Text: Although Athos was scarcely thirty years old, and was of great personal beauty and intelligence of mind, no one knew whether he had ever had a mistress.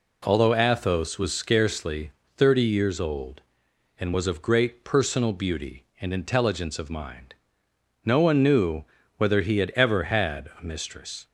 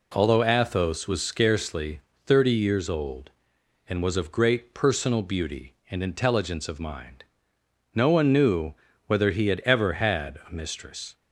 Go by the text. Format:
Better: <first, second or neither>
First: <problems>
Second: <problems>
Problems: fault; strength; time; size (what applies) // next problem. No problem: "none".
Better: neither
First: pauses between "scarcely" and "thirty"; slight; at 2.1 s; 0.26 s long // pauses between "knew" and "whether"; slight; at 8.8 s; 0.32 s long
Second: pauses between "scarcely" and "thirty"; slight; at 2.0 s; 0.26 s long // pauses between "knew" and "whether"; slight; at 8.7 s; 0.32 s long